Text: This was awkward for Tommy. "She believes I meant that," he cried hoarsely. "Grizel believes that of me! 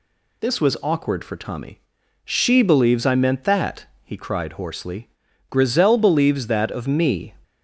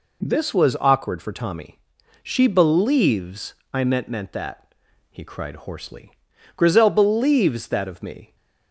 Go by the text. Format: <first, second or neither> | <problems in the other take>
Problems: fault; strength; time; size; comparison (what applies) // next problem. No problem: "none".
first | pauses between "believes" and "I"; slight; at 3.5 s; 0.18 s long // says "meant" twice; at 4.0 s